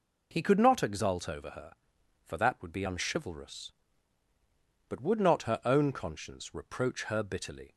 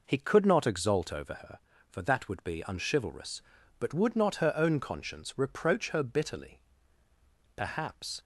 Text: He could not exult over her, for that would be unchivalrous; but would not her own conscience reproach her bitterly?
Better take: first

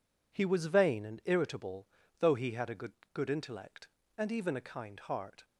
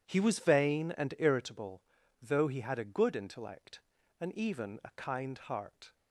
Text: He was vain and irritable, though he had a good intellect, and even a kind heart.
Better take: second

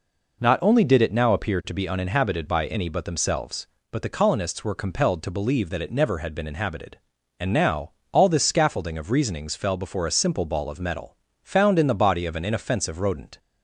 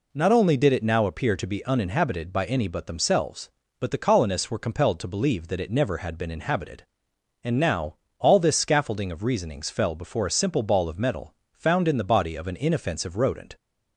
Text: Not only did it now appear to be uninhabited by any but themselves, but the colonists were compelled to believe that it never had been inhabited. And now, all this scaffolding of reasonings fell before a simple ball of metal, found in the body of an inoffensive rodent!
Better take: neither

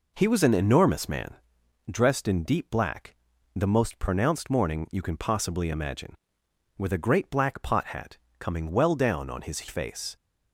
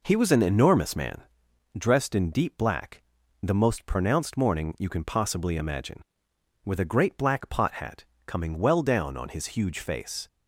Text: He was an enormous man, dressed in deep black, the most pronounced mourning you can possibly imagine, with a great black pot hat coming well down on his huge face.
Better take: second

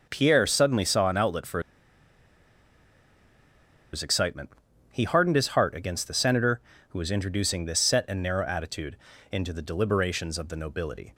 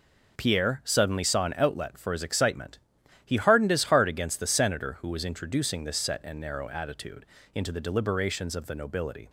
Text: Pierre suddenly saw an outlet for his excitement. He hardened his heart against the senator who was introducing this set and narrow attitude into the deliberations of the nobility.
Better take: second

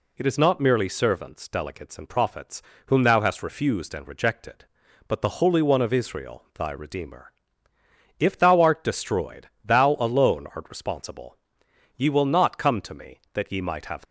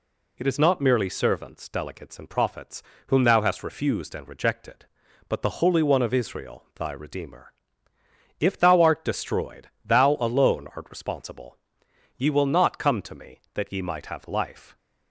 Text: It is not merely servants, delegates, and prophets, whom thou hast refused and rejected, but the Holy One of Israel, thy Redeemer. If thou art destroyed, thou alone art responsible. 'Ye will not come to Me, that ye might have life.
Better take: second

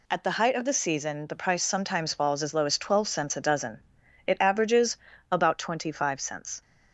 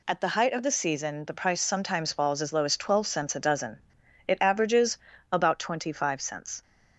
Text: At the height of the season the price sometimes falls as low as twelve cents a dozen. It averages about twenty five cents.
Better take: neither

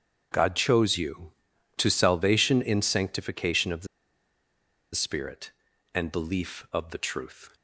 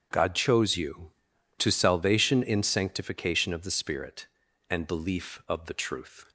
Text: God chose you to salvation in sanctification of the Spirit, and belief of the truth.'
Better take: second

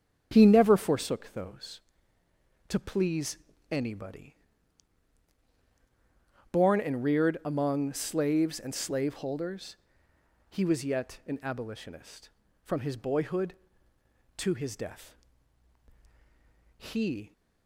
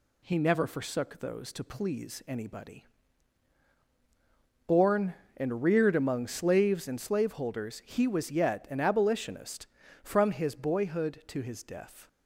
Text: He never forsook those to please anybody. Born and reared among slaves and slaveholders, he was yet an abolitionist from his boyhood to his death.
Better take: second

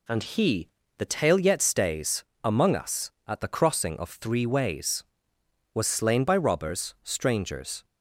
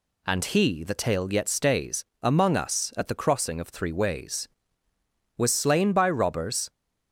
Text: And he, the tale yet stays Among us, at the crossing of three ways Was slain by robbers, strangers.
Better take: first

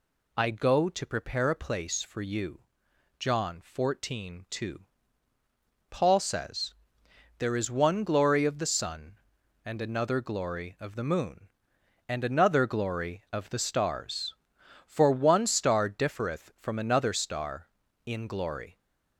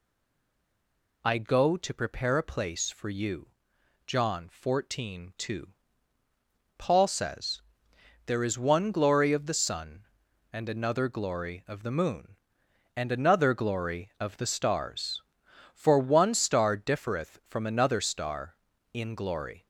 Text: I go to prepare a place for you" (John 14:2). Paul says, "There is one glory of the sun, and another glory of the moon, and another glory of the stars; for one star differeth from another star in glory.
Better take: first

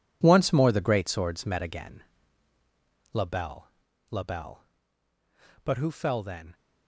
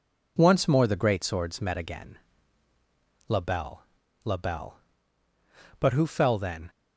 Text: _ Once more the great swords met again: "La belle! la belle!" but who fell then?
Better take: second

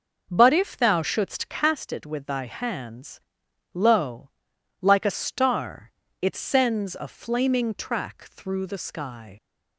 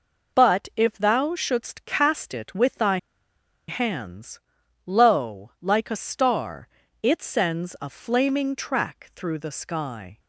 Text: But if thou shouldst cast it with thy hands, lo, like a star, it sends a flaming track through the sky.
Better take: first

